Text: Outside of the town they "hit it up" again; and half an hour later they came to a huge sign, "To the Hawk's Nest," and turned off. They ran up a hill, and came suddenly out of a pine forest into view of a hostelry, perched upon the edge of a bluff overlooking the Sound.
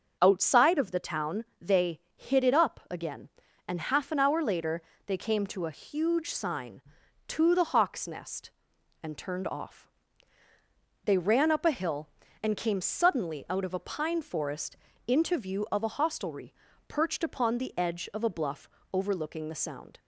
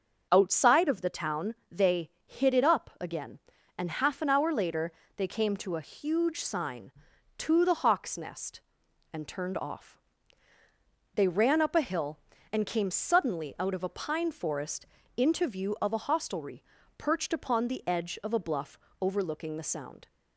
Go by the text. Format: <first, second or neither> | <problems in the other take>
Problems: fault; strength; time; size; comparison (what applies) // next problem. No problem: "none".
neither | starts louder than the rest; the same in both // pauses between "town" and "they"; slight; the same in both // pauses between "they" and "hit"; slight; the same in both // pauses between "later" and "they"; slight; the same in both // pauses between "forest" and "into"; slight; the same in both // pauses between "bluff" and "overlooking"; slight; the same in both